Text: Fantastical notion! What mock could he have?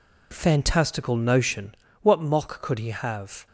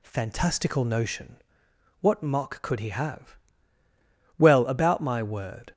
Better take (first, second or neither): first